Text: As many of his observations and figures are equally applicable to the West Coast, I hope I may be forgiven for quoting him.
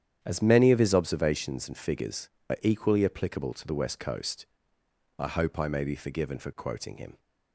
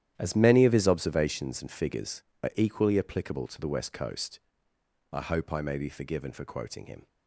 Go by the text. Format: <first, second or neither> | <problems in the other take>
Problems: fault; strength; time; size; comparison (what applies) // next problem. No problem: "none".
first | gets quieter; strong; throughout; 13.5 dB // starts louder than the rest; strong; until 1.1 s; 11 dB; strong in the first